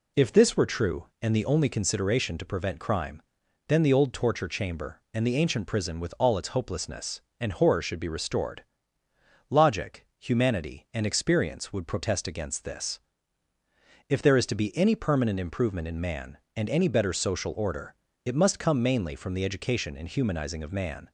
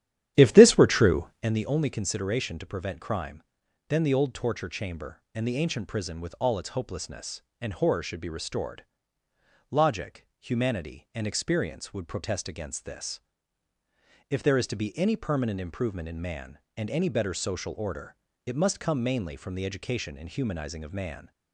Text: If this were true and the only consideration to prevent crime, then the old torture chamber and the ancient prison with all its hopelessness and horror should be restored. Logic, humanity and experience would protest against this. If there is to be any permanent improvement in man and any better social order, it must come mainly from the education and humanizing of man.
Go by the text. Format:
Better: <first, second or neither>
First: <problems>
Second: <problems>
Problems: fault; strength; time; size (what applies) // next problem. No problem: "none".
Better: first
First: none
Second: starts louder than the rest; strong; until 1.5 s; 11.5 dB